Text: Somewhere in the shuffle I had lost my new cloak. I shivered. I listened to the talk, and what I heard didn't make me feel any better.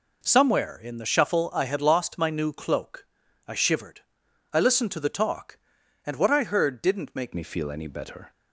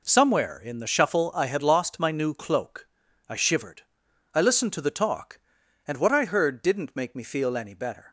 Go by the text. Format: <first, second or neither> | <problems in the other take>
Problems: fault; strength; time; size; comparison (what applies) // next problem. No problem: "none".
second | changes voice at "me"; from 7.3 s on; 1.0 s long